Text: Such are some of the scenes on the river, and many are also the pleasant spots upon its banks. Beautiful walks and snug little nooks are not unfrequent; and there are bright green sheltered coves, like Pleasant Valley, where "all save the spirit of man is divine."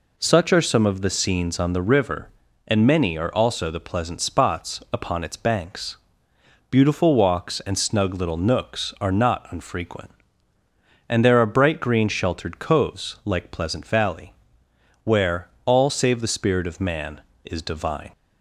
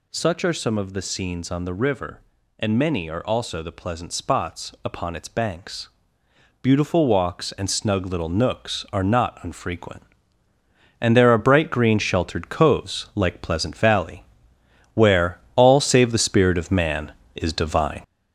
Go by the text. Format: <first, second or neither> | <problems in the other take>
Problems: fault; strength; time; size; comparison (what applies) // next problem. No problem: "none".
first | gets louder; noticeable; throughout; 6 dB // pauses between "where" and "all"; slight; at 15.3 s; 0.18 s long; slight in the first